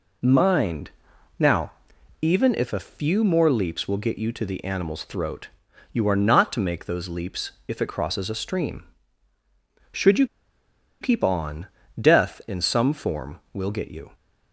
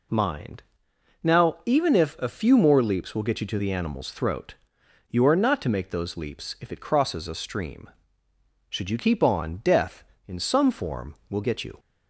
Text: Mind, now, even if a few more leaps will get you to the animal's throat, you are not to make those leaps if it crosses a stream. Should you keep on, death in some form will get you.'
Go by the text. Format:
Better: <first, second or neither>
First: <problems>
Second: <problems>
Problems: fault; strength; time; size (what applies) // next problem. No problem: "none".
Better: second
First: pauses between "leaps" and "if"; slight; at 7.5 s; 0.16 s long // pauses between "you" and "keep"; noticeable; at 10.2 s; 0.75 s long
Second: none